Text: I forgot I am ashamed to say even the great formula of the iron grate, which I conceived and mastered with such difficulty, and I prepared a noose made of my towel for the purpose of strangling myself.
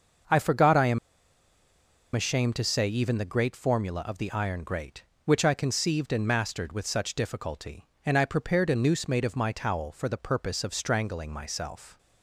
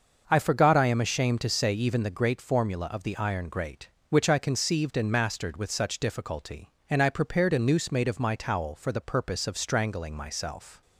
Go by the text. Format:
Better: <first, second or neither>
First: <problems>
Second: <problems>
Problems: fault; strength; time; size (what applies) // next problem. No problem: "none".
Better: second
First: starts louder than the rest; until 2.4 s; 6.5 dB // pauses between "am" and "ashamed"; at 0.9 s; 1.1 s long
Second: starts louder than the rest; until 1.2 s; 6.5 dB